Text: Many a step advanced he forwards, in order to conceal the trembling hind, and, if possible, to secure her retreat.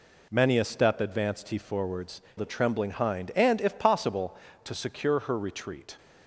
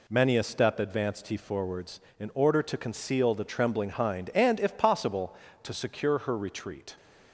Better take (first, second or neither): second